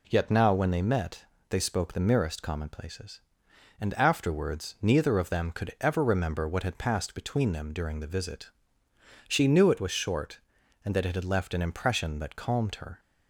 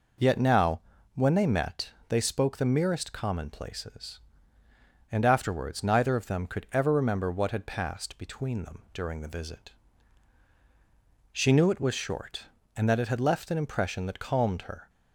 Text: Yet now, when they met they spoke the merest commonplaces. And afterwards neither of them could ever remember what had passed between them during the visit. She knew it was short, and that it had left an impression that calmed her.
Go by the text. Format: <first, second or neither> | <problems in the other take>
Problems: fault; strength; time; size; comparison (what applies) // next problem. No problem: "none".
neither | pauses between "met" and "they"; slight; the same in both